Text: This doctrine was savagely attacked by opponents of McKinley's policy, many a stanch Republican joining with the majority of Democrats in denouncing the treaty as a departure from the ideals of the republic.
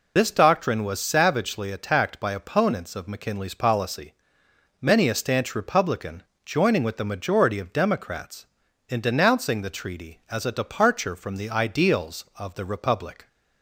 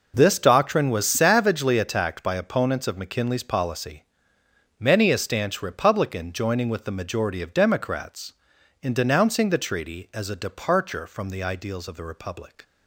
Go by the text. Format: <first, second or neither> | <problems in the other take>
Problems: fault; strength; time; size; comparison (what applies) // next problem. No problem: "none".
second | loses the start of "This"; at 0.1 s; 105 ms // pauses between "Republican" and "joining"; slight; at 6.2 s; 0.20 s long